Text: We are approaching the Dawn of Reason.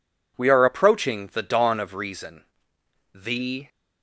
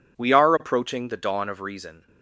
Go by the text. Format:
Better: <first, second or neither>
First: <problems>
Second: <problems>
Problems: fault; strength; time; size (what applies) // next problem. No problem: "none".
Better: second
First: goes on to say "THE"; from 3.1 s on; 0.54 s long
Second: none